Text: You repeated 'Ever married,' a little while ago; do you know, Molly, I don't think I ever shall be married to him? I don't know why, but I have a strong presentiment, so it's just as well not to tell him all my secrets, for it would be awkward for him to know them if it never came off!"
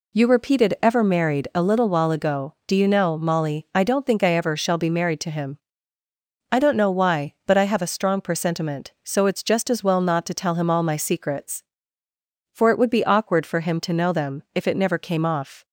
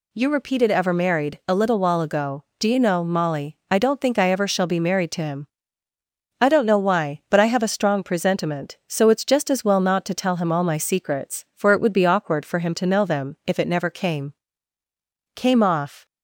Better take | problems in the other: first | says "came" twice; at 15.3 s

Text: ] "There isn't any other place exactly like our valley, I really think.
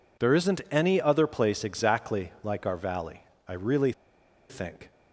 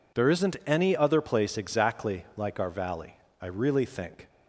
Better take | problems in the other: second | pauses between "really" and "think"; noticeable; at 3.9 s; 0.58 s long

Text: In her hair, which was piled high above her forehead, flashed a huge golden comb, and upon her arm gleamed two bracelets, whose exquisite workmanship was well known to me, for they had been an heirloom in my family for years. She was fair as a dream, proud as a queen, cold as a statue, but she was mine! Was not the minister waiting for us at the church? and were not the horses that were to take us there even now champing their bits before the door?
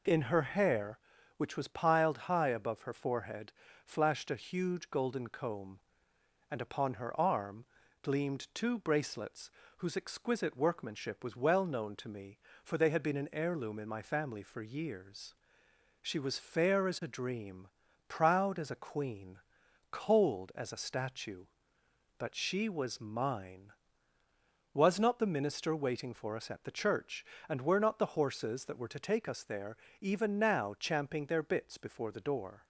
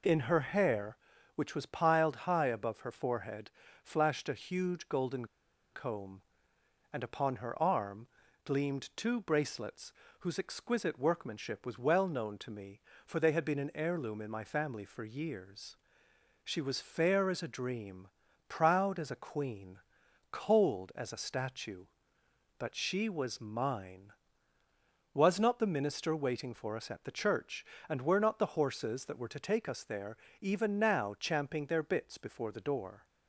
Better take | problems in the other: first | pauses between "golden" and "comb"; noticeable; at 5.2 s; 0.47 s long // pauses between "arm" and "gleamed"; at 8.0 s; 0.38 s long; also in the first // pauses between "there" and "even"; slight; at 30.1 s; 0.24 s long; slight in the first

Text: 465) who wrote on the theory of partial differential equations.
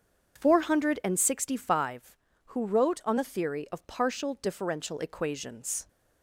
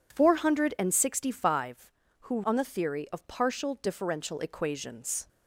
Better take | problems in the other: first | skips "wrote"; at 2.4 s

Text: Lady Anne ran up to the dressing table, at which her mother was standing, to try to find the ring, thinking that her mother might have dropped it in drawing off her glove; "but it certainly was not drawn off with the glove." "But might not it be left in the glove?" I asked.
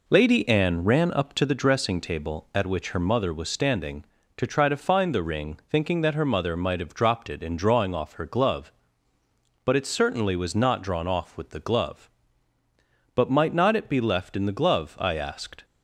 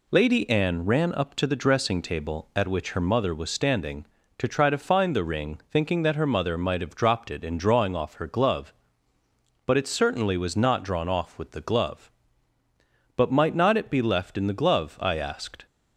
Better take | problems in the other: second | starts louder than the rest; noticeable; until 1.7 s; 4 dB

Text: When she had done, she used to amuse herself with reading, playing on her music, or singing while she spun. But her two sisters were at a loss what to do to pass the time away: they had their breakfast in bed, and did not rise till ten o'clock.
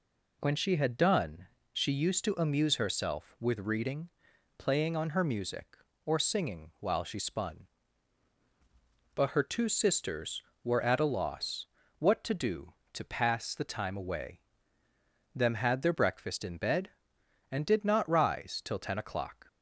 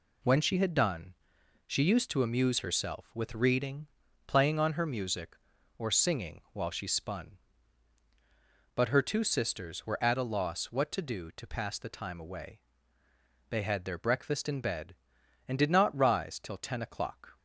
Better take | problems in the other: second | pauses between "loss" and "what"; slight; at 11.6 s; 0.34 s long // says "them" for "they"; at 15.3 s

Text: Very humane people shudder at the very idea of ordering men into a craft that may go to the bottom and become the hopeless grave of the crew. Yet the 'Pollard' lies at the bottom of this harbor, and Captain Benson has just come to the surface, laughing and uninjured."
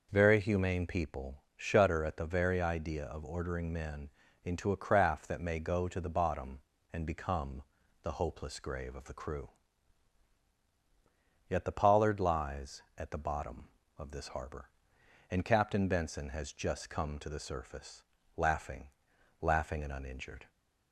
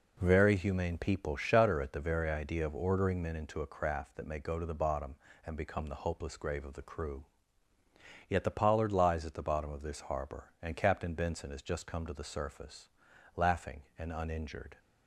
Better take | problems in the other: second | pauses between "men" and "into"; slight; at 4.0 s; 0.34 s long // pauses between "become" and "the"; at 7.6 s; 0.40 s long // says "laughing" twice; at 19.4 s

